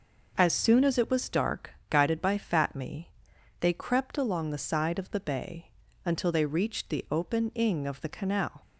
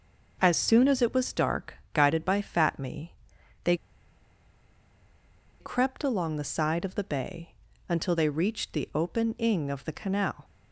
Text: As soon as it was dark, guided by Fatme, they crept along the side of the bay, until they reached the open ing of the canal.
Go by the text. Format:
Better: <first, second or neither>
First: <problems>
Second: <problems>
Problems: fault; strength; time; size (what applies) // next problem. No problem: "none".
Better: first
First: none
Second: pauses between "they" and "crept"; strong; at 3.7 s; 1.8 s long